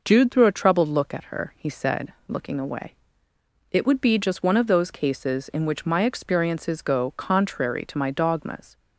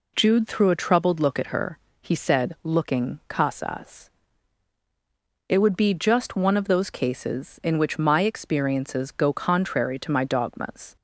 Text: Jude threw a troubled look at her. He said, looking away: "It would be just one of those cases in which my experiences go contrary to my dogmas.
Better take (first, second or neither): first